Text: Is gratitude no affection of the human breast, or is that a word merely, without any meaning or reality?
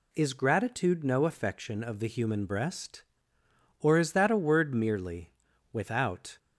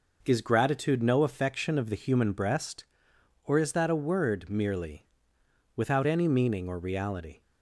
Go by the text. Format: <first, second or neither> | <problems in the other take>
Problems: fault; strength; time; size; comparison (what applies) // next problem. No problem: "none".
second | stops before "any meaning or reality"; at 6.3 s